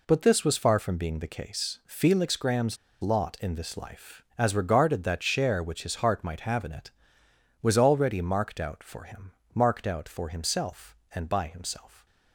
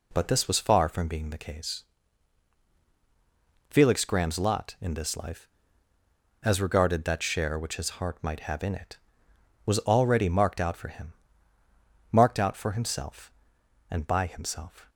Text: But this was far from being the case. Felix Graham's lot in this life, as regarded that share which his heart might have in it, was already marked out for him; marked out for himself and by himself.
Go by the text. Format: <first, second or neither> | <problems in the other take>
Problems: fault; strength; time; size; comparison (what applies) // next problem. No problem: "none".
second | pauses between "Graham's" and "lot"; slight; at 2.7 s; 0.24 s long